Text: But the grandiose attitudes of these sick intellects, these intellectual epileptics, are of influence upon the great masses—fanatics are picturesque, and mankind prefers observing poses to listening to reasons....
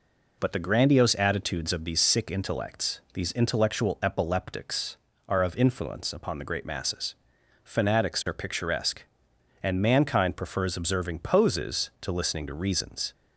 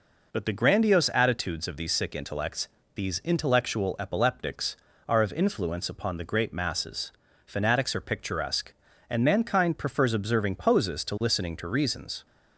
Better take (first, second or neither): neither